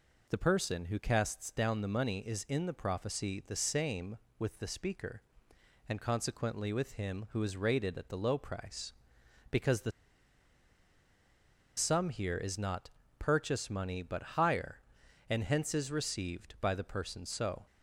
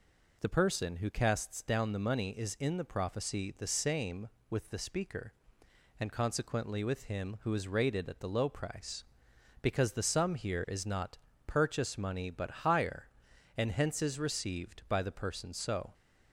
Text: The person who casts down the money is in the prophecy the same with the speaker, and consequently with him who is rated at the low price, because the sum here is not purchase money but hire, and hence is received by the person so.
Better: second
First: pauses between "the" and "sum"; strong; at 9.9 s; 1.8 s long // pauses between "not" and "purchase"; slight; at 12.9 s; 0.26 s long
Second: pauses between "not" and "purchase"; slight; at 11.1 s; 0.26 s long

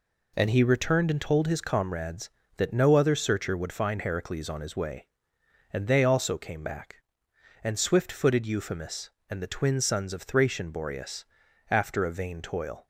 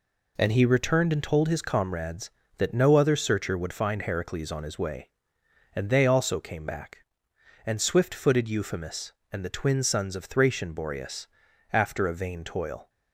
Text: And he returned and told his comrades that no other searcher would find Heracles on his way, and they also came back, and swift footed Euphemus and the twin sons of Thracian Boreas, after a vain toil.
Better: neither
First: none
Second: none

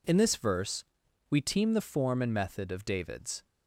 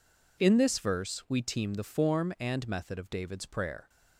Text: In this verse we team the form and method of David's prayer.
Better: second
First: pauses between "verse" and "we"; noticeable; at 0.8 s; 0.48 s long // stops before "prayer"; at 3.4 s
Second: none

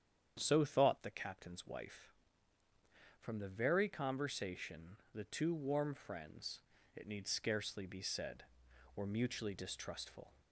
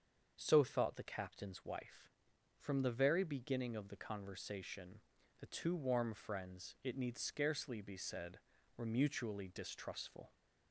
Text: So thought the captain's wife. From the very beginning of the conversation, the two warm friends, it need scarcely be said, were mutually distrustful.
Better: second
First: starts louder than the rest; strong; until 1.4 s; 9 dB // skips "beginning of the"; at 3.8 s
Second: starts louder than the rest; until 1.3 s; 7 dB

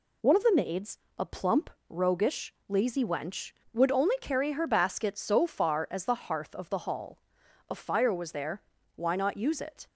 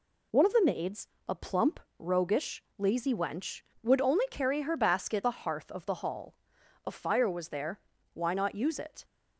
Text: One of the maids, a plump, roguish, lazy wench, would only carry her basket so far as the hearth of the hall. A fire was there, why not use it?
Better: first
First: none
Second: skips "so far as"; at 5.2 s

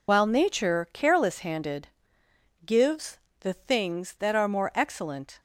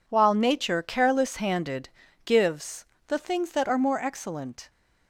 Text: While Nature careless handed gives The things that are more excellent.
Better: second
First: loses the start of "While"; at 0.0 s; 60 ms // pauses between "handed" and "gives"; noticeable; at 1.8 s; 0.80 s long // pauses between "gives" and "The"; slight; at 3.1 s; 0.22 s long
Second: pauses between "handed" and "gives"; slight; at 1.8 s; 0.36 s long // pauses between "gives" and "The"; slight; at 2.8 s; 0.22 s long

